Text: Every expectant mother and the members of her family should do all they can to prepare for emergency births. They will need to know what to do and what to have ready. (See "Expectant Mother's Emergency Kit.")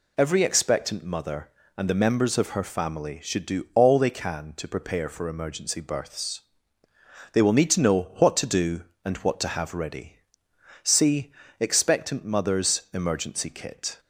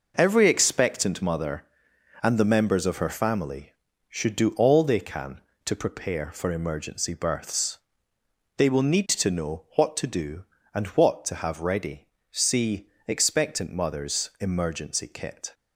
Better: neither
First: pauses between "See" and "Expectant"; slight; at 11.3 s; 0.28 s long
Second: pauses between "See" and "Expectant"; slight; at 12.8 s; 0.18 s long

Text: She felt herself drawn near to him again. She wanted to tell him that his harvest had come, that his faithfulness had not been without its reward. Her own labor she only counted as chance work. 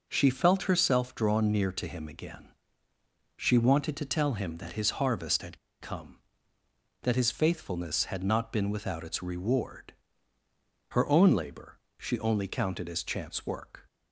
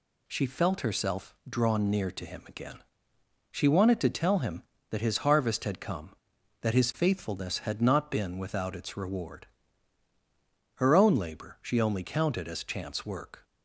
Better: second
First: pauses between "had" and "come"; slight; at 5.5 s; 0.23 s long // pauses between "labor" and "she"; slight; at 11.7 s; 0.20 s long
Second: none

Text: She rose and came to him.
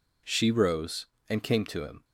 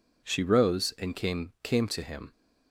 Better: first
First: none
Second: says "came" twice; at 1.6 s

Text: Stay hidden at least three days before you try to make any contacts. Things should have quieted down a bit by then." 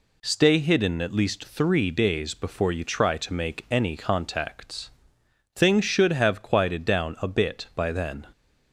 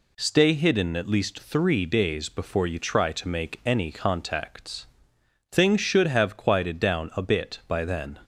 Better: neither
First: none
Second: none

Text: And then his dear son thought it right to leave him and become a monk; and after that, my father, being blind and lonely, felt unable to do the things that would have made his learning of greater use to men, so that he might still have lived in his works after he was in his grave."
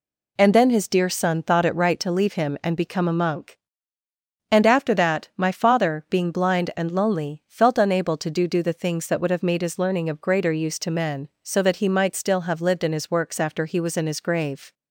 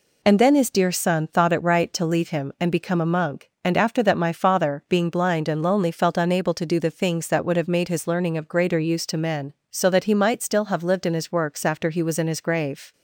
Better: second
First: says "do" twice; at 8.4 s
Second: none

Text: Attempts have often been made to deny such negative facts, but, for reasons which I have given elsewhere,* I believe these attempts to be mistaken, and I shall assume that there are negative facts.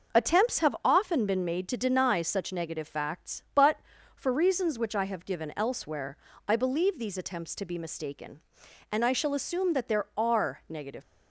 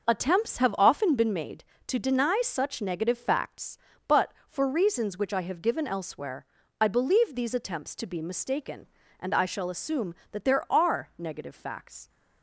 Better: second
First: stops before "facts"; at 11.0 s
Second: none

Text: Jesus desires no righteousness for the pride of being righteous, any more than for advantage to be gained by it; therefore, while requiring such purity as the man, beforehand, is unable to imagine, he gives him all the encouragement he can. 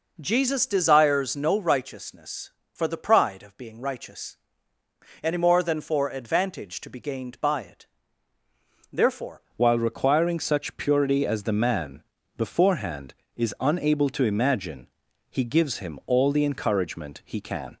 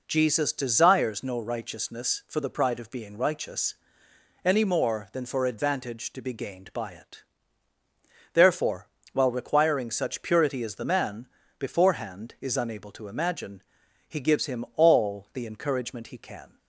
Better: second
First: changes voice at "while"; from 9.5 s on; 8.2 s long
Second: none

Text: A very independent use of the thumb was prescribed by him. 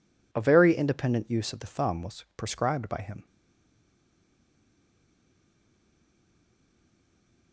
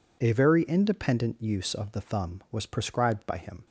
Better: second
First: stays silent after the last word; strong; from 3.2 s on; 4.3 s long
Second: none

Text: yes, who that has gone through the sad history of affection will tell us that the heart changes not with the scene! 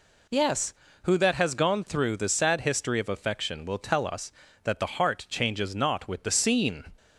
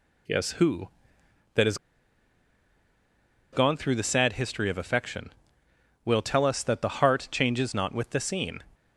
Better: first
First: none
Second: pauses between "has" and "gone"; strong; at 1.7 s; 1.7 s long

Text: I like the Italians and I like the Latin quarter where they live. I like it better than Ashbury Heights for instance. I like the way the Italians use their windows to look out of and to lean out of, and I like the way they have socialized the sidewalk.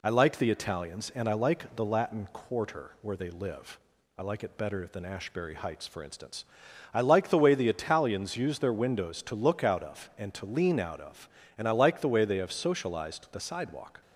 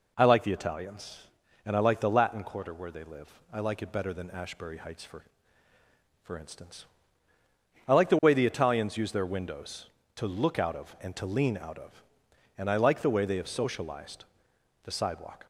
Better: first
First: none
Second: says "for" twice; at 6.2 s // pauses between "socialized" and "the"; noticeable; at 14.2 s; 0.60 s long

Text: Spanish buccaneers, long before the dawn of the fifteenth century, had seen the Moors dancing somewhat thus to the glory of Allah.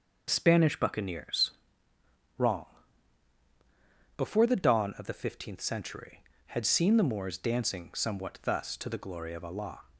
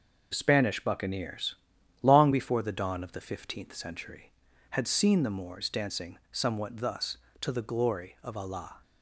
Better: second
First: says "wrong" for "long"; at 2.3 s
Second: none

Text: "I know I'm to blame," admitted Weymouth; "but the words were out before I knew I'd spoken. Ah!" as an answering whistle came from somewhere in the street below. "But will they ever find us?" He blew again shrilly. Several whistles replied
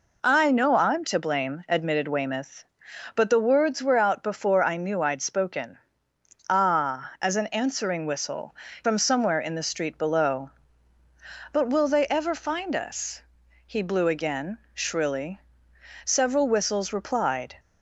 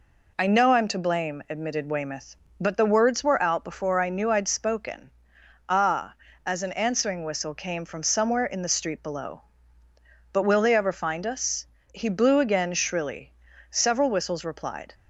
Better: second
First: skips "came"; at 8.6 s // pauses between "again" and "shrilly"; slight; at 14.5 s; 0.16 s long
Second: none

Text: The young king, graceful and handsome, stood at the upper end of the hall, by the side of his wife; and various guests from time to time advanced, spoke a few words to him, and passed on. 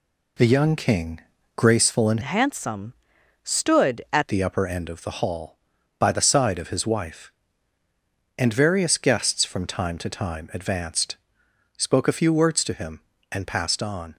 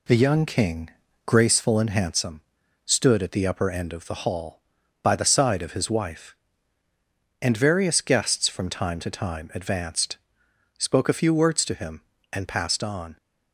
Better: second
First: changes voice from "handsome" to "at"; from 2.2 to 4.2 s; 2.0 s long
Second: none

